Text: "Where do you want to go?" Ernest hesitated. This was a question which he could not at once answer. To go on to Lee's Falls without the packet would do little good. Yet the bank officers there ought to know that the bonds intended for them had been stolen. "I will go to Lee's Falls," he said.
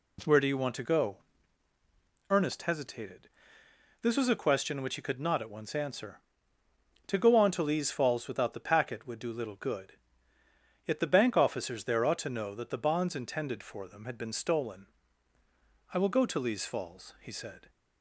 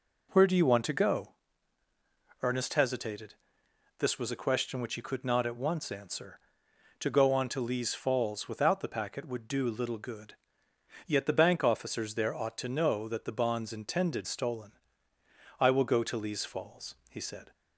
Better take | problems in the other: first | skips "for them had been"; at 14.2 s

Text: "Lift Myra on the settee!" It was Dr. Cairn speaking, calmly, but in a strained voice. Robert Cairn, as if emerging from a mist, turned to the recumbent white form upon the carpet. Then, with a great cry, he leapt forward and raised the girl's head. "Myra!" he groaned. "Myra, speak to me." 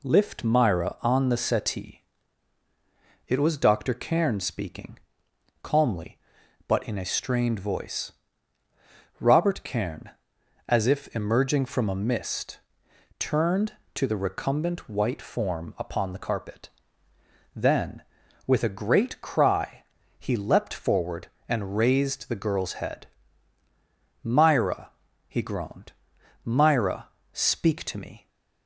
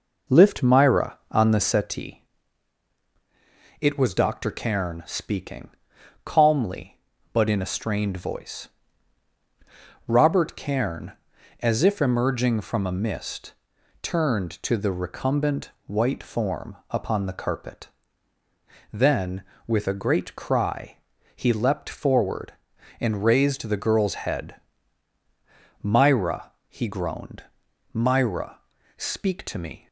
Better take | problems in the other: first | starts louder than the rest; noticeable; until 1.9 s; 5 dB // pauses between "recumbent" and "white"; slight; at 15.6 s; 0.16 s long

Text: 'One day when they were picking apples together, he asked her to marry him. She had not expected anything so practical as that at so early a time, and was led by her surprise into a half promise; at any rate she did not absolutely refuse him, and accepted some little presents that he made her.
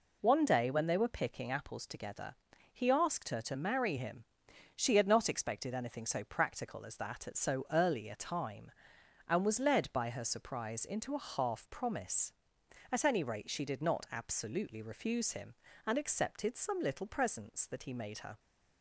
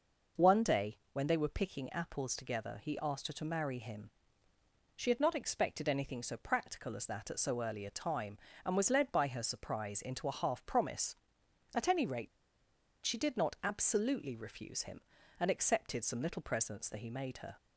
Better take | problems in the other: first | pauses between "day" and "when"; slight; at 0.9 s; 0.16 s long // pauses between "rate" and "she"; noticeable; at 12.2 s; 0.77 s long

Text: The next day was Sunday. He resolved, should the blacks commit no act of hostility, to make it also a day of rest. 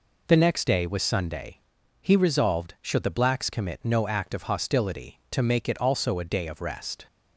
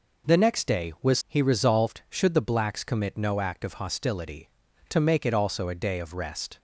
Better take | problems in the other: first | skips "Sunday"; at 1.2 s

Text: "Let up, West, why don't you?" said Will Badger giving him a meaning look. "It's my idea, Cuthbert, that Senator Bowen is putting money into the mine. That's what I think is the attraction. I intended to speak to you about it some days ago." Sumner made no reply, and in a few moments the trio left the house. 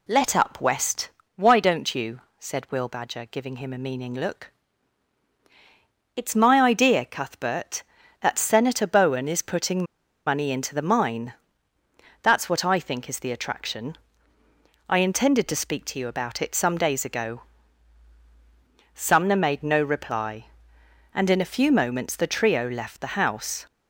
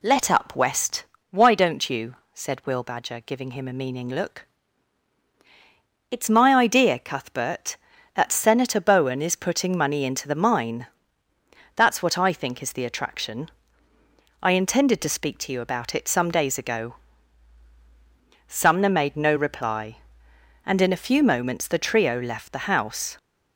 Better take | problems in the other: second | pauses between "putting" and "money"; at 9.8 s; 0.43 s long

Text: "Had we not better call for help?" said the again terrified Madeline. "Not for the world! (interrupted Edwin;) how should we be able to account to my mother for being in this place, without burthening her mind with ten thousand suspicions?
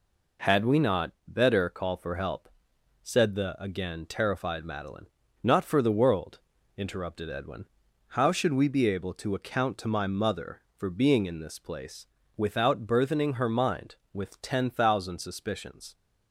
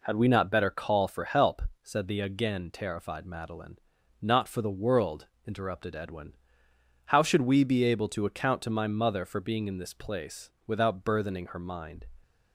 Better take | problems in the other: first | stops before "with ten thousand suspicions"; at 12.2 s

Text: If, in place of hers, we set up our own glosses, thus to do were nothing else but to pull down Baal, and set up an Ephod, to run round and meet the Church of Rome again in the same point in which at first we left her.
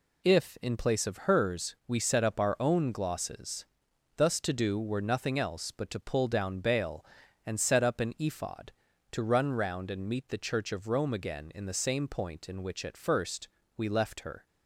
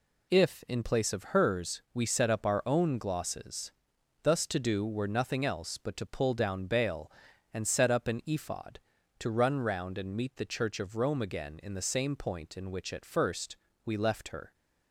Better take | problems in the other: neither | pauses between "first" and "we"; slight; the same in both

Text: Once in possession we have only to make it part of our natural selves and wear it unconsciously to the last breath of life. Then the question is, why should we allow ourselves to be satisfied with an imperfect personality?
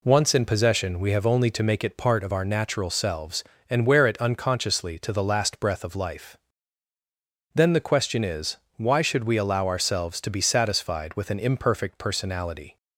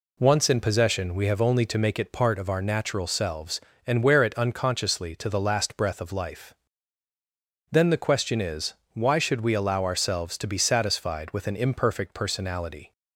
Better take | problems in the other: neither | none

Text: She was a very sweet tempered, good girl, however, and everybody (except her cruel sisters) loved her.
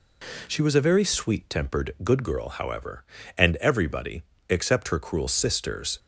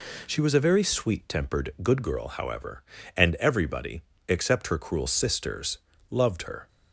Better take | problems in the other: second | stops before "loved her"; at 5.9 s

